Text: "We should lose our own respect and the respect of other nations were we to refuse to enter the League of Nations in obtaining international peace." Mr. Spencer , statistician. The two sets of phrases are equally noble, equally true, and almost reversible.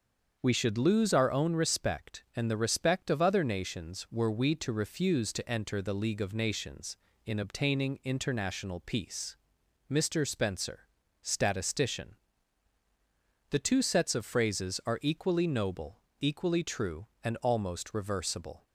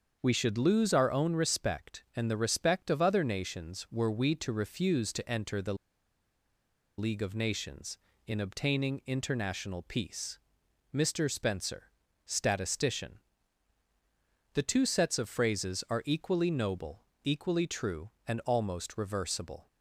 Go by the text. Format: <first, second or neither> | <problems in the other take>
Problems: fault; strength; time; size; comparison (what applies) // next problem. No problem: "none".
first | starts louder than the rest; until 1.2 s; 7 dB; also in the first // pauses between "the" and "League"; at 5.7 s; 1.2 s long